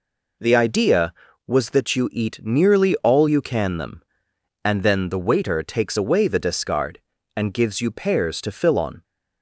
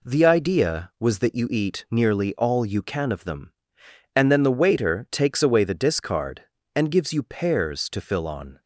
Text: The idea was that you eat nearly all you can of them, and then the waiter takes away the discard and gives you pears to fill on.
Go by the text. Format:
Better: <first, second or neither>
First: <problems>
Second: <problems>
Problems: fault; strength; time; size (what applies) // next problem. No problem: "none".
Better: second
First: skips "of"; at 3.7 s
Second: none